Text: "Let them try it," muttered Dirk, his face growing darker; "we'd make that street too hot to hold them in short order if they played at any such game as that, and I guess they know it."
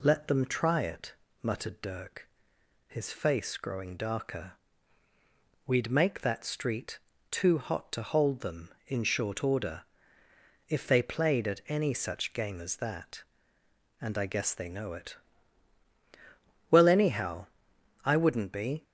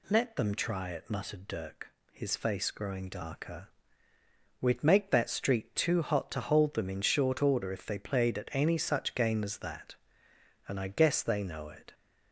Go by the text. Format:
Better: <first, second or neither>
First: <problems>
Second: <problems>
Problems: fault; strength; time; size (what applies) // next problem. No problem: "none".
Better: second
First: pauses between "street" and "too"; slight; at 6.9 s; 0.32 s long // pauses between "order" and "if"; noticeable; at 9.8 s; 0.86 s long // goes on to say "Well anyhow I wouldn't be"; strong; from 16.7 s on; 2.1 s long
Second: none